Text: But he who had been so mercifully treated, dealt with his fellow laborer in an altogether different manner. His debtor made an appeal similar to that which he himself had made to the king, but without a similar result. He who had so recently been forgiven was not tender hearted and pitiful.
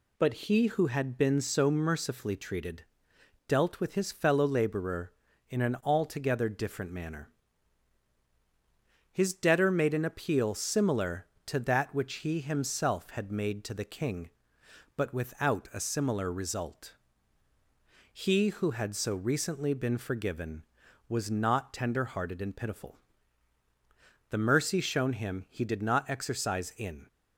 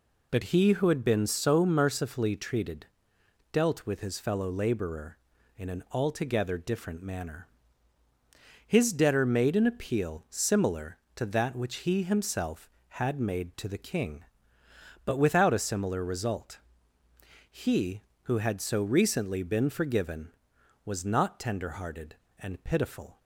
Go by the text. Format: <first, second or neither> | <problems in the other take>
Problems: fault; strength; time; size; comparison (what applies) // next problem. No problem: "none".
second | goes on to say "The mercy shown him he did not exercise in"; strong; from 24.3 s on; 2.7 s long